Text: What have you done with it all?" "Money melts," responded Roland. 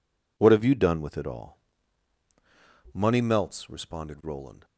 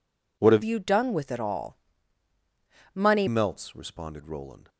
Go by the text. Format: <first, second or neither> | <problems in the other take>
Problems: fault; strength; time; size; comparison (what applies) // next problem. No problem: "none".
first | changes voice from "you" to "Money"; from 0.6 to 3.2 s; 2.6 s long